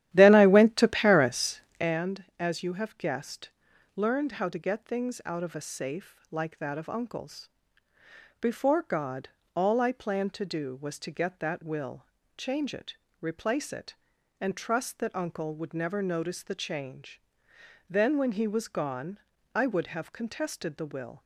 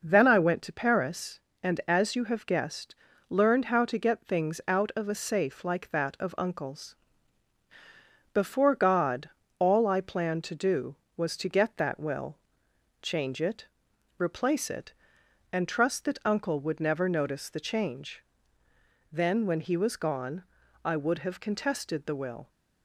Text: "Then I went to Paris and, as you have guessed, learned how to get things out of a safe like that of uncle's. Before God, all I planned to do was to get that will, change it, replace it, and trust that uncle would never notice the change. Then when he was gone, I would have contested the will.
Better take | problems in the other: second | starts louder than the rest; strong; until 2.0 s; 12.5 dB

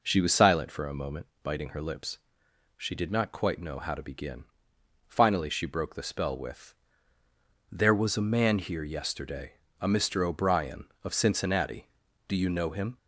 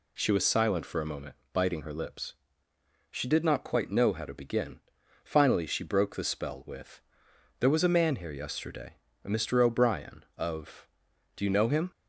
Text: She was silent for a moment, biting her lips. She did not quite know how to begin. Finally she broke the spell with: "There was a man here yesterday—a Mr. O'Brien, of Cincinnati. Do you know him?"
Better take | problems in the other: first | skips "Cincinnati"; at 11.1 s

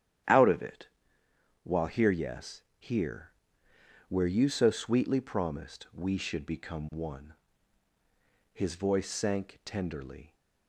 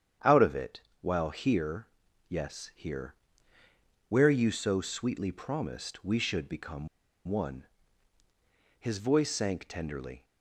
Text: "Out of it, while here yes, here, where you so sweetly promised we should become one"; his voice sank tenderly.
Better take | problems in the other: first | starts louder than the rest; strong; until 1.4 s; 9 dB; strong in the first // pauses between "here" and "yes"; at 1.8 s; 0.40 s long // pauses between "become" and "one"; at 6.8 s; 0.40 s long

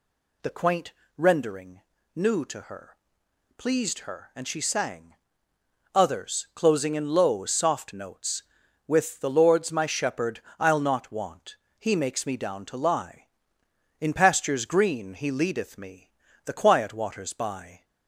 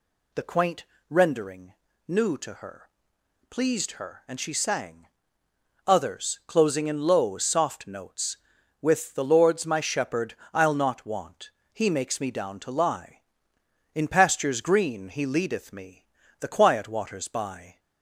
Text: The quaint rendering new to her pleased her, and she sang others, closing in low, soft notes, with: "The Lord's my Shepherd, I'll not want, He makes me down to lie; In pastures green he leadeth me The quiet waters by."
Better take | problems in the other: neither | pauses between "quaint" and "rendering"; slight; the same in both // pauses between "rendering" and "new"; slight; the same in both // pauses between "her" and "pleased"; noticeable; the same in both // pauses between "sang" and "others"; noticeable; the same in both // pauses between "me" and "The"; slight; the same in both

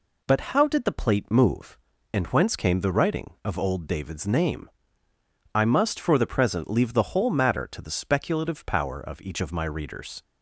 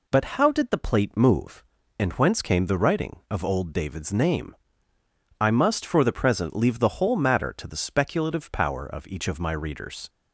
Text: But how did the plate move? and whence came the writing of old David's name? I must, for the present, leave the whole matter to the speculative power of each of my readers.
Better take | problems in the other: neither | none

